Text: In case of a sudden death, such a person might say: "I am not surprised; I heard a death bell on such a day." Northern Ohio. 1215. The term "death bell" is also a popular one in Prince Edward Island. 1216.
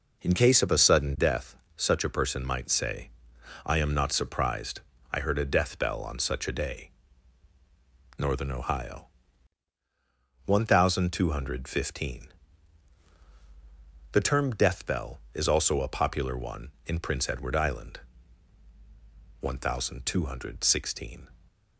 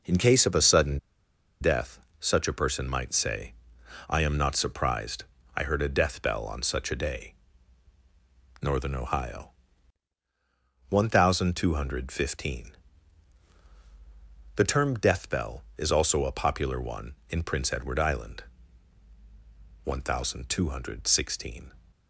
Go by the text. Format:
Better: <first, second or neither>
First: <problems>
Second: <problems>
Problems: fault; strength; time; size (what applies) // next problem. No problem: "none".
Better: first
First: none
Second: pauses between "sudden" and "death"; noticeable; at 0.9 s; 0.63 s long